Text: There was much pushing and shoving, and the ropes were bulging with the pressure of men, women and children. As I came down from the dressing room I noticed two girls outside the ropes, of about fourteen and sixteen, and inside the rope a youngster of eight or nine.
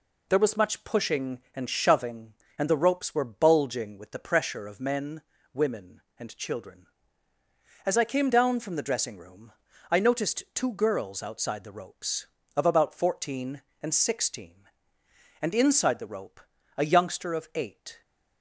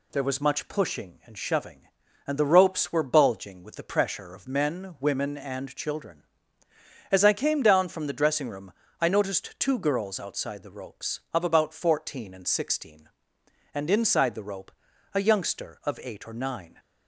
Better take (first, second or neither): second